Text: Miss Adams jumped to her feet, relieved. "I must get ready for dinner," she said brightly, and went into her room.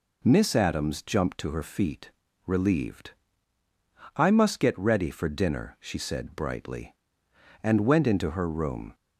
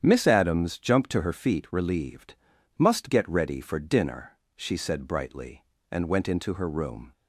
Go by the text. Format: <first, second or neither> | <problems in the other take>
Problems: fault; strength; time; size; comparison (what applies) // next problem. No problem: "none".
first | starts louder than the rest; strong; until 1.0 s; 9 dB // skips "I"; at 2.5 s